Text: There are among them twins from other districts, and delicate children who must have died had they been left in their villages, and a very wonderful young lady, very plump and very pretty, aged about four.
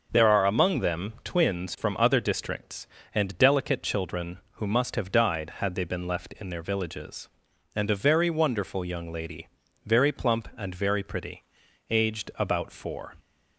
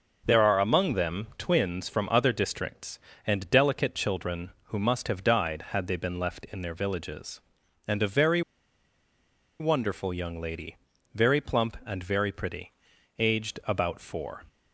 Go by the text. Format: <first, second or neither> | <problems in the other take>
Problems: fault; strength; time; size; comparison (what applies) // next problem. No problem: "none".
first | starts louder than the rest; noticeable; until 1.2 s; 6 dB; noticeable in the first // pauses between "very" and "wonderful"; at 8.4 s; 1.1 s long